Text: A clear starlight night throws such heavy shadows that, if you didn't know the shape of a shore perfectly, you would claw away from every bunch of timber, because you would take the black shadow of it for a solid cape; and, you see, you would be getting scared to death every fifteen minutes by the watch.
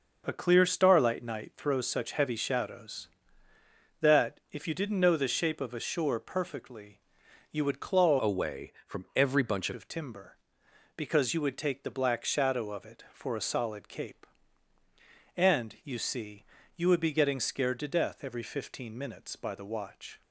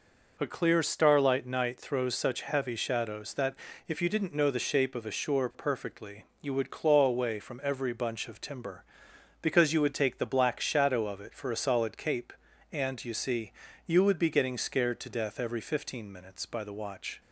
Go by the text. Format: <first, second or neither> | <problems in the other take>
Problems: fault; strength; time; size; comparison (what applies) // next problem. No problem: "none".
second | changes voice from "away" to "bunch"; from 8.2 to 9.7 s; 1.5 s long